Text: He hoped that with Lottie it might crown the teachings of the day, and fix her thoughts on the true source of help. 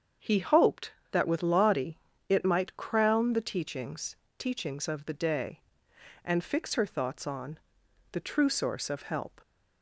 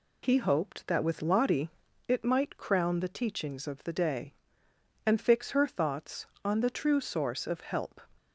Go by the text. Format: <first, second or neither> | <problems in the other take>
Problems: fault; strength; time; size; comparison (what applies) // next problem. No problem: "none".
second | starts louder than the rest; until 1.4 s; 7 dB // pauses between "Lottie" and "it"; slight; at 1.9 s; 0.30 s long; also in the second // says "teachings" twice; at 4.3 s // pauses between "on" and "the"; noticeable; at 7.5 s; 0.54 s long